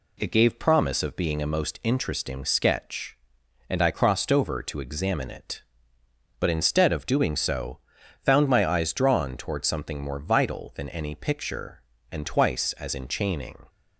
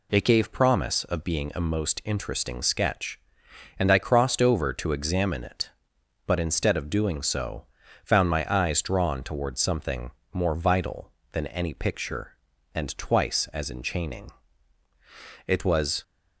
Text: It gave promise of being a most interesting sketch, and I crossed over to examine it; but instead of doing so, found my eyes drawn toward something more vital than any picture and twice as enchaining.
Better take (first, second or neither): first